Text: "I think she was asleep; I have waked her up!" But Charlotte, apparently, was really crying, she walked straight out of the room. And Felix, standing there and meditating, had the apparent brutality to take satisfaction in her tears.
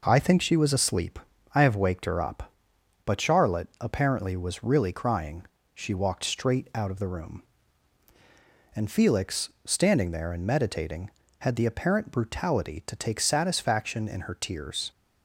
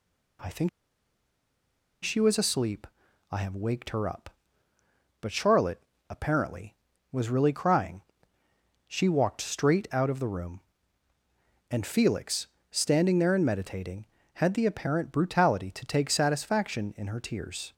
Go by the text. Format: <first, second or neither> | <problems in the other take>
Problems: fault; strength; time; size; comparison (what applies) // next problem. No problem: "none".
first | pauses between "think" and "she"; strong; at 0.6 s; 1.3 s long